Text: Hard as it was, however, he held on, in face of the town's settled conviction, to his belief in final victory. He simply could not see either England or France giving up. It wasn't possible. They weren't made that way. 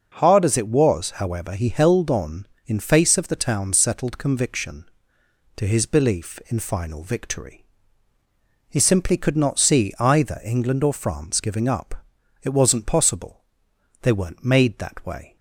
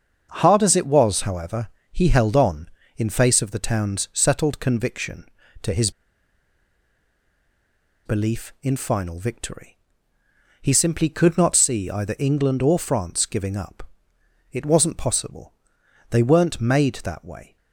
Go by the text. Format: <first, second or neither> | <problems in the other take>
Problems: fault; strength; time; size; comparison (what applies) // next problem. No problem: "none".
first | starts louder than the rest; until 1.3 s; 6.5 dB // pauses between "his" and "belief"; strong; at 5.8 s; 2.1 s long